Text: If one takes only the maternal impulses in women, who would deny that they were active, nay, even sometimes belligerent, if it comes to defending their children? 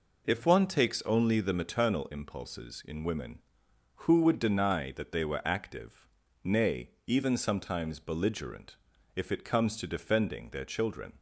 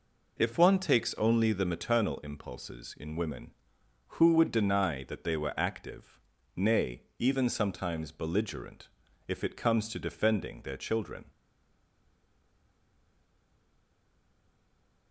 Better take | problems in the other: first | stays silent after the last word; strong; from 11.2 s on; 3.9 s long

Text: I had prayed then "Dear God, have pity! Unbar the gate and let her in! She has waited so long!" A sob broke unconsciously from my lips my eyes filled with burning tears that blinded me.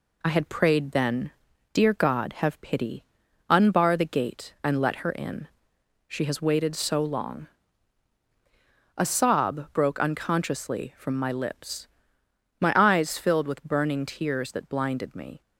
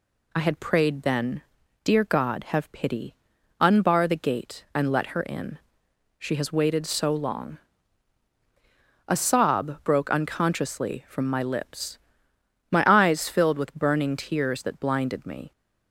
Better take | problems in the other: second | gets quieter; slight; throughout; 2.5 dB // pauses between "then" and "Dear"; at 1.3 s; 0.42 s long; also in the second // pauses between "lips" and "my"; noticeable; at 11.8 s; 0.76 s long; noticeable in the second

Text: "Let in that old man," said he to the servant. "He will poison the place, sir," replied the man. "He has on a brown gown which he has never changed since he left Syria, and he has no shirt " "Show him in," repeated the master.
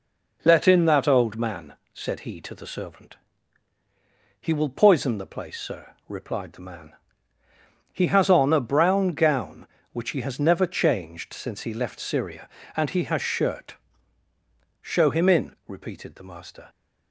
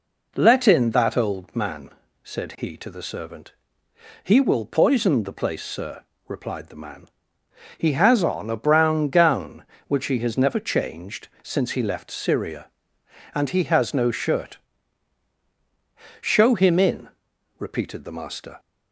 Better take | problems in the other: second | skips "no"; at 13.2 s

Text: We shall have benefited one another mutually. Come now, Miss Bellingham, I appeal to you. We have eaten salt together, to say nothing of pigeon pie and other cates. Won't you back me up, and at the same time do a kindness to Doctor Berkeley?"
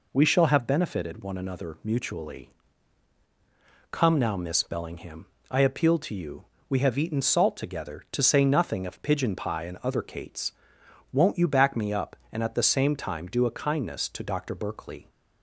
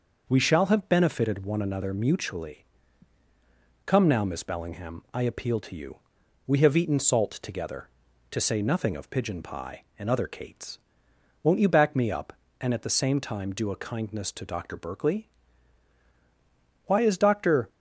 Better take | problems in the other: first | starts louder than the rest; noticeable; until 1.2 s; 6 dB // goes on to say "Why is Doctor"; noticeable; from 16.8 s on; 0.82 s long

